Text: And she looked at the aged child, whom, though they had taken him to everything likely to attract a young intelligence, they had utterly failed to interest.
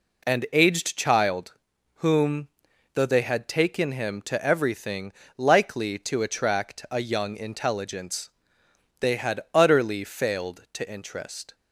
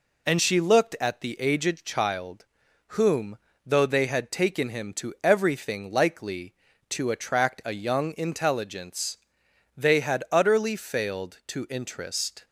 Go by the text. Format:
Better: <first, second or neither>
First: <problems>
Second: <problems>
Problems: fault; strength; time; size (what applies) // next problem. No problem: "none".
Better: second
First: skips "she looked at the"; at 0.4 s // pauses between "everything" and "likely"; slight; at 5.1 s; 0.24 s long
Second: none